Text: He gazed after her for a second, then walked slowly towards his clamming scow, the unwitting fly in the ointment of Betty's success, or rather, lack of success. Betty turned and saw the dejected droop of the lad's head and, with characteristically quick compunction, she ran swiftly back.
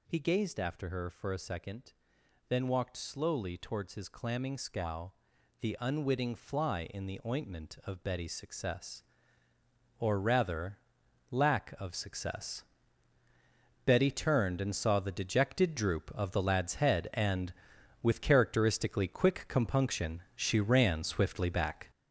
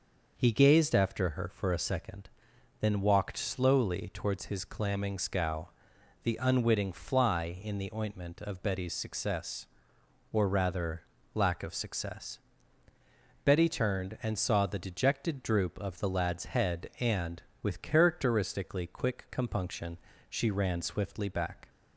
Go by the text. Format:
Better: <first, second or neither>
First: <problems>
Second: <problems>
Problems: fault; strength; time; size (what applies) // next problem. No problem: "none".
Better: second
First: gets louder; throughout; 7 dB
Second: none